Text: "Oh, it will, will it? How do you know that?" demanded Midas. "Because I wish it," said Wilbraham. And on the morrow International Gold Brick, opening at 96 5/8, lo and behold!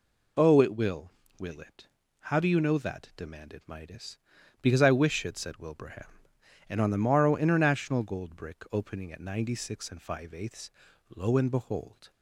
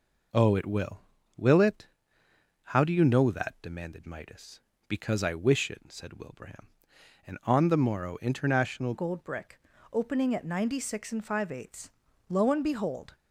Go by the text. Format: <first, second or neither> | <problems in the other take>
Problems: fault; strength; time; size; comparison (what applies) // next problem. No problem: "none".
first | changes voice at "Gold"; from 8.9 s on; 4.2 s long